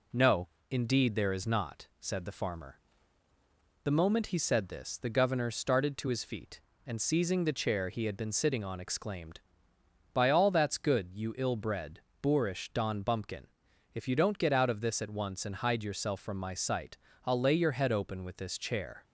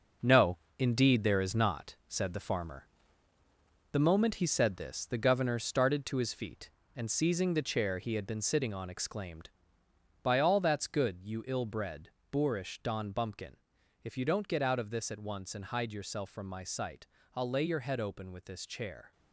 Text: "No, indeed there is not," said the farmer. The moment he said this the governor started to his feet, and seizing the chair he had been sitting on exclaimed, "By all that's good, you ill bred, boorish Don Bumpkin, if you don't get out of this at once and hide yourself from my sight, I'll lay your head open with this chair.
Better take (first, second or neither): first